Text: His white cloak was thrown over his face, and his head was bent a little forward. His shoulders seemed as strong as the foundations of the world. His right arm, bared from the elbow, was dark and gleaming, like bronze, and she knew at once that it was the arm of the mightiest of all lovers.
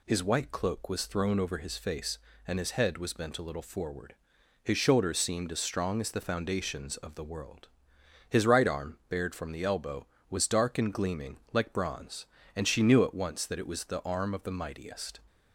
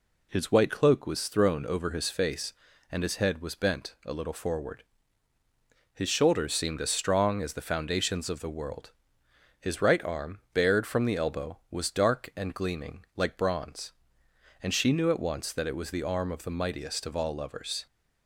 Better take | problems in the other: second | stops before "of all lovers"; at 15.2 s

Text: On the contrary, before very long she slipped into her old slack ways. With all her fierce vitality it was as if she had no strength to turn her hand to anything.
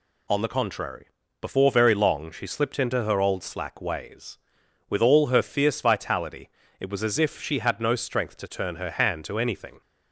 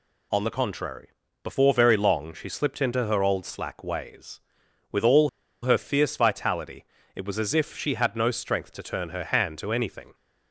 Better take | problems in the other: first | pauses between "all" and "her"; slight; at 5.2 s; 0.33 s long // pauses between "vitality" and "it"; slight; at 6.8 s; 0.30 s long; slight in the first

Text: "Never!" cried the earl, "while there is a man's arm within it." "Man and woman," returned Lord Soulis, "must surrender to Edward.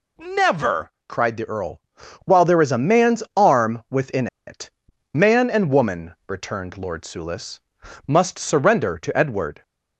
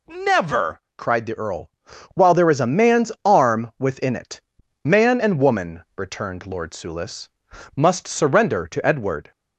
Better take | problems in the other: second | pauses between "within" and "it"; slight; at 4.2 s; 0.20 s long

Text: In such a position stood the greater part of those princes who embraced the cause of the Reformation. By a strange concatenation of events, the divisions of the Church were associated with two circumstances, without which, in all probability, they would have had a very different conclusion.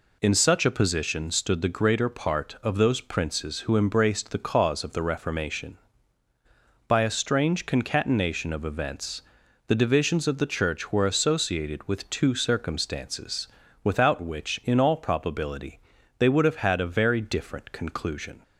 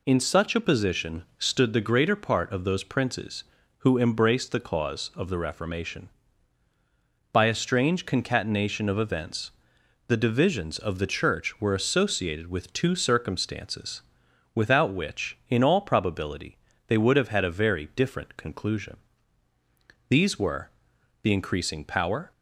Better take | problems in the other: first | goes on to say "These were the increasing power"; strong; from 20.0 s on; 2.2 s long

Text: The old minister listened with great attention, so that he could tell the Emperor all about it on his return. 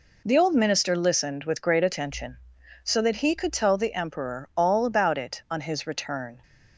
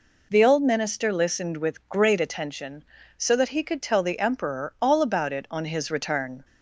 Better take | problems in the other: neither | none

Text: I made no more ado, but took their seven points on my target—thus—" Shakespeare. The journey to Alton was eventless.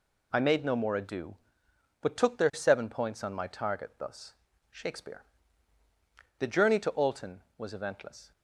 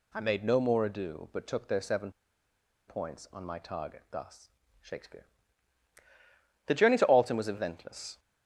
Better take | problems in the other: first | pauses between "seven" and "points"; noticeable; at 2.0 s; 0.78 s long

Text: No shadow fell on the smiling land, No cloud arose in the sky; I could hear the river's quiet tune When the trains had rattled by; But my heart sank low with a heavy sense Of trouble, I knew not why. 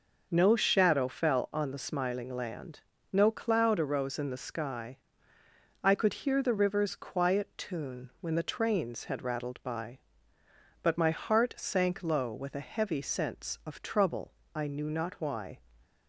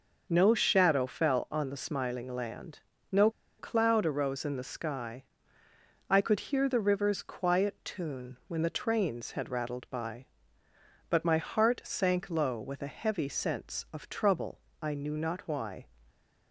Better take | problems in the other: first | pauses between "No" and "cloud"; slight; at 3.2 s; 0.30 s long

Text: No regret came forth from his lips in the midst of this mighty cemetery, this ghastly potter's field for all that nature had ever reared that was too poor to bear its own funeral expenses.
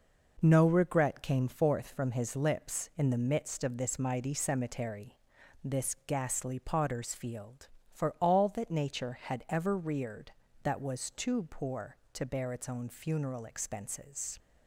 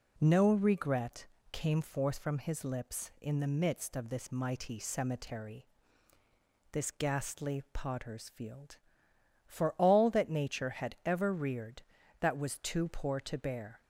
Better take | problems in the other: first | pauses between "regret" and "came"; slight; at 1.2 s; 0.24 s long // stops before "its own funeral expenses"; at 13.8 s

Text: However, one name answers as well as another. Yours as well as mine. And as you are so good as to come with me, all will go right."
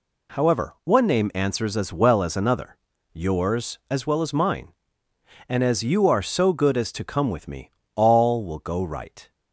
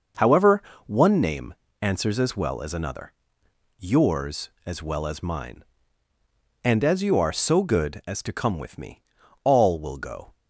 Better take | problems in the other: first | pauses between "name" and "answers"; slight; at 1.5 s; 0.26 s long // stops before "right"; at 10.3 s

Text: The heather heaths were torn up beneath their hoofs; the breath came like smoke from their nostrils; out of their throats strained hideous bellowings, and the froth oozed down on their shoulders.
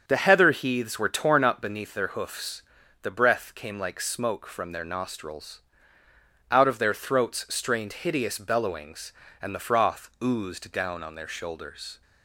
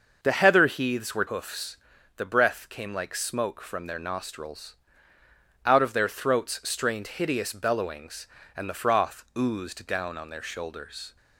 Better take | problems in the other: first | starts louder than the rest; noticeable; until 1.2 s; 6 dB; also in the first // skips "torn up beneath their"; at 1.2 s

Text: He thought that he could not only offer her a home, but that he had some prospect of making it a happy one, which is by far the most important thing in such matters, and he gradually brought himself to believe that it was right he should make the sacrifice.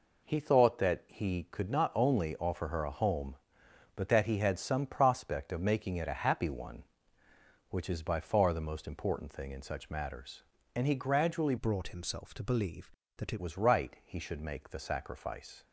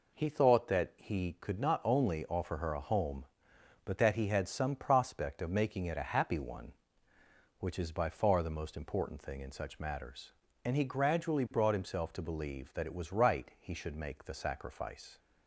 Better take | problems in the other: second | changes voice from "brought" to "it"; from 11.5 to 13.4 s; 1.9 s long

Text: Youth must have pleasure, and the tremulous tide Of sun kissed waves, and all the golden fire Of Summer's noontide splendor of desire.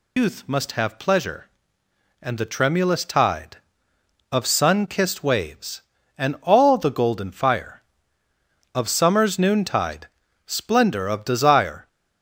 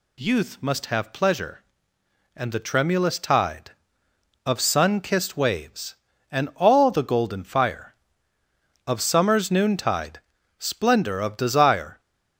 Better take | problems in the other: second | loses the start of "Youth"; at 0.1 s; 125 ms // pauses between "noontide" and "splendor"; at 10.0 s; 0.40 s long; also in the second

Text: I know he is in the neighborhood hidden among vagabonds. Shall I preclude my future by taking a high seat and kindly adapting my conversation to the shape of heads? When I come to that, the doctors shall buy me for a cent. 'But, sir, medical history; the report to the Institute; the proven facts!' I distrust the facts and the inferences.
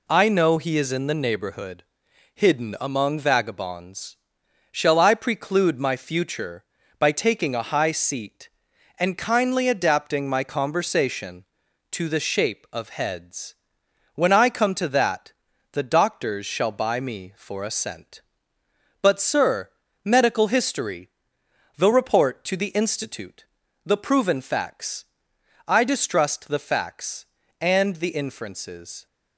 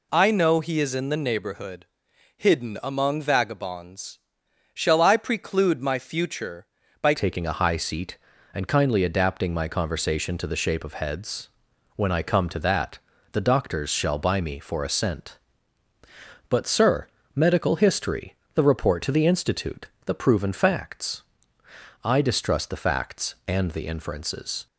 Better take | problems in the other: first | pauses between "neighborhood" and "hidden"; noticeable; at 1.8 s; 0.52 s long; noticeable in the first // changes voice at "taking"; from 7.1 s on; 17.5 s long

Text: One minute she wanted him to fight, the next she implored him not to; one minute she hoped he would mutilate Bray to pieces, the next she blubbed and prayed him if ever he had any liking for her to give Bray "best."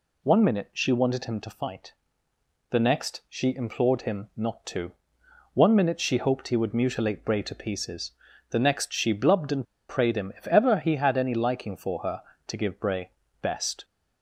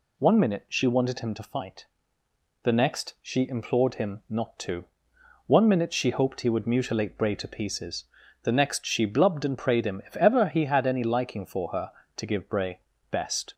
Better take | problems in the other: second | pauses between "and" and "prayed"; slight; at 9.6 s; 0.24 s long // pauses between "Bray" and "best"; slight; at 13.1 s; 0.30 s long; slight in the second

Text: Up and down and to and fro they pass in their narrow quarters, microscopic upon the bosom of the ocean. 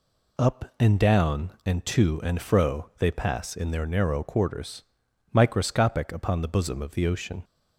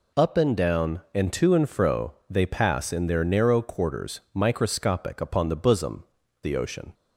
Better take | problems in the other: first | pauses between "fro" and "they"; slight; at 2.1 s; 0.16 s long // skips "of"; at 6.2 s

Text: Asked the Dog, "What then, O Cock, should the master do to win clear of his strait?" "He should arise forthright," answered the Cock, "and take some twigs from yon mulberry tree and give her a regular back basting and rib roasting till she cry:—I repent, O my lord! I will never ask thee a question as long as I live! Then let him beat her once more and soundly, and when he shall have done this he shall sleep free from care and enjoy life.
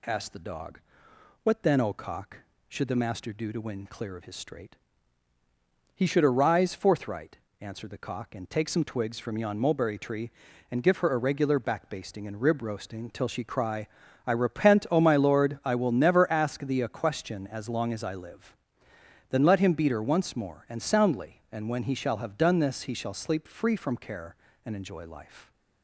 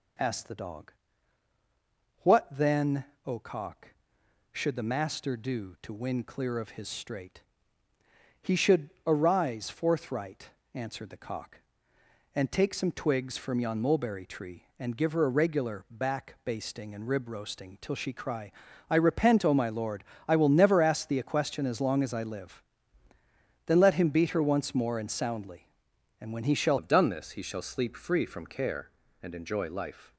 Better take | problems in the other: first | pauses between "should" and "arise"; slight; at 8.8 s; 0.16 s long // changes voice at "have"; from 26.7 s on; 3.4 s long

